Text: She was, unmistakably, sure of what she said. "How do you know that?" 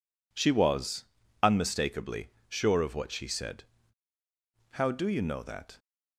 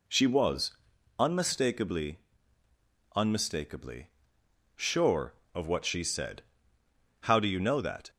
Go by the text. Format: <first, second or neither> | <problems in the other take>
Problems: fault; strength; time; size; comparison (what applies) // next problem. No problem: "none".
first | says "unmistakably" twice; at 3.1 s